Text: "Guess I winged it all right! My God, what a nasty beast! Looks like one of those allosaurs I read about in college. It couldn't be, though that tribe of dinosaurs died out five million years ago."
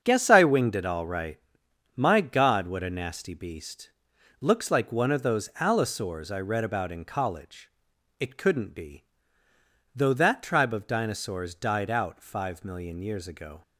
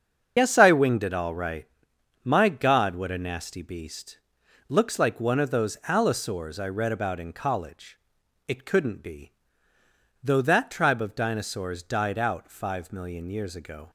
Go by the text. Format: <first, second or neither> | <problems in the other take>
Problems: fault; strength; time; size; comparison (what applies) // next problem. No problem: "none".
first | loses the start of "Guess"; at 0.3 s; 50 ms // starts louder than the rest; until 1.3 s; 7 dB; strong in the first